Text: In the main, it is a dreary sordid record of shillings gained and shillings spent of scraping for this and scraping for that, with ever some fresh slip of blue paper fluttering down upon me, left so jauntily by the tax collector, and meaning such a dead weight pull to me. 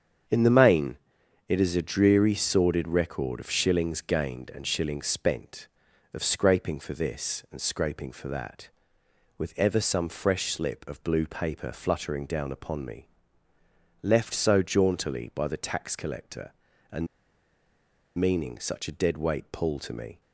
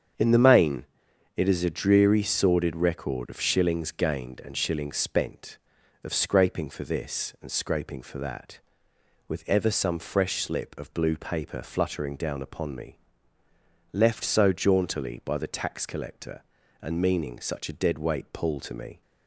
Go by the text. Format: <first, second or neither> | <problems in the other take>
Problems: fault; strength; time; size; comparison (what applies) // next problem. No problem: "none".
second | starts louder than the rest; strong; until 1.7 s; 7.5 dB; strong in the second // pauses between "and" and "meaning"; at 17.0 s; 1.1 s long